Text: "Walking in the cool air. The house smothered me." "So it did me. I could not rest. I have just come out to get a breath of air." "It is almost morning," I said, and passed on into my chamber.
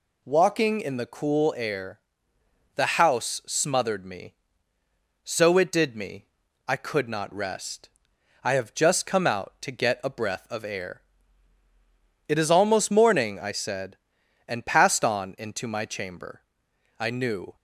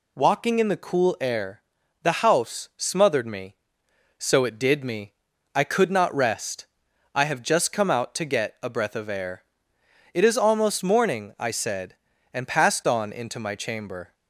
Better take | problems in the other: second | goes on to say "I knew"; from 16.9 s on; 0.56 s long

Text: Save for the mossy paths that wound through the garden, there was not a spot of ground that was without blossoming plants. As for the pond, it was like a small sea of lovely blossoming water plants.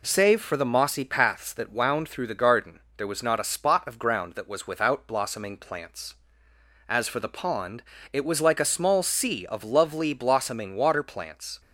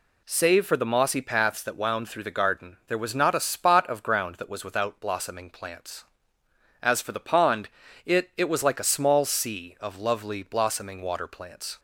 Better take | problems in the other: first | says "it" twice; at 8.3 s

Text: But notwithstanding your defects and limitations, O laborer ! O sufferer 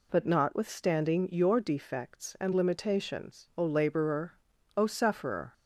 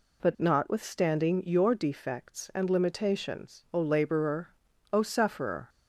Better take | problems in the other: neither | none

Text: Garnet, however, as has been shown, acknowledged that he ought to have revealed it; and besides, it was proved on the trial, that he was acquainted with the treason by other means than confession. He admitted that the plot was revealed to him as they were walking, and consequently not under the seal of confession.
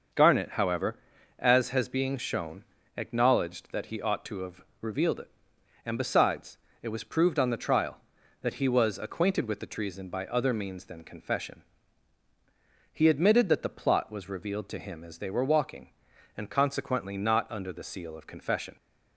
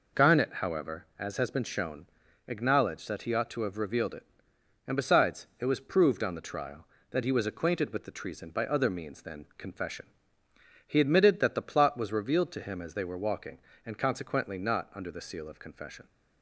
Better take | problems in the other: second | starts louder than the rest; until 1.5 s; 6 dB // says "being" for "been"; at 1.8 s // pauses between "have" and "revealed"; slight; at 4.6 s; 0.20 s long

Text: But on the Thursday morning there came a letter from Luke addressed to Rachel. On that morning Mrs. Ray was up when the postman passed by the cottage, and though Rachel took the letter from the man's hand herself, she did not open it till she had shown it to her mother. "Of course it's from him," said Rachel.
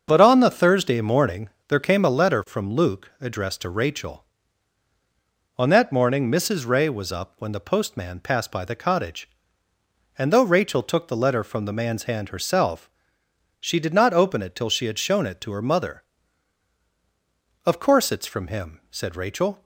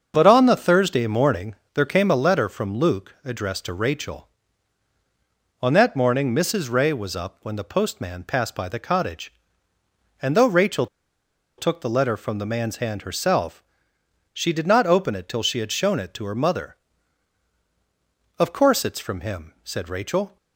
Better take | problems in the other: first | starts louder than the rest; until 1.1 s; 6.5 dB; also in the first // pauses between "morning" and "there"; slight; at 1.5 s; 0.18 s long; slight in the first // pauses between "Rachel" and "took"; noticeable; at 10.8 s; 0.72 s long

